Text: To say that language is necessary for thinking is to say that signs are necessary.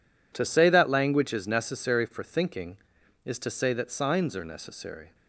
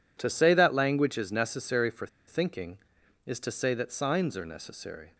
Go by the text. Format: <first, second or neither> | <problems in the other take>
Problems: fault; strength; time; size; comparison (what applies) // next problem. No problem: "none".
first | pauses between "for" and "thinking"; slight; at 2.0 s; 0.20 s long